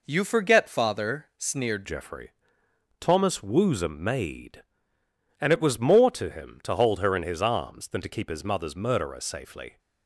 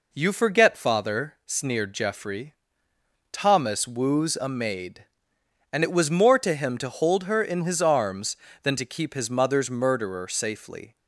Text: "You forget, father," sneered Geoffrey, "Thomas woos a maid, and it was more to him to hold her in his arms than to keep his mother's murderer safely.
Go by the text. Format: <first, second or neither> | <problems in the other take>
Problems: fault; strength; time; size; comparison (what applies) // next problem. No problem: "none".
second | changes voice at "Geoffrey"; from 1.8 s on; 7.9 s long